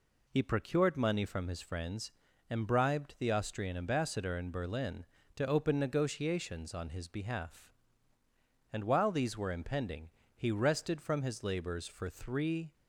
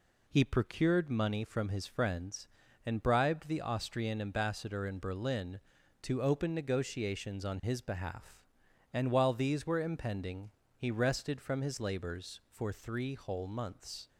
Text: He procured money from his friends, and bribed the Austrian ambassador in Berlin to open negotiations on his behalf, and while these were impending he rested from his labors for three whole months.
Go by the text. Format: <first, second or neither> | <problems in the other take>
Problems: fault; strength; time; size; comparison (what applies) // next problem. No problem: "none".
second | pauses between "impending" and "he"; slight; at 10.0 s; 0.26 s long; slight in the second // stops before "whole months"; at 12.7 s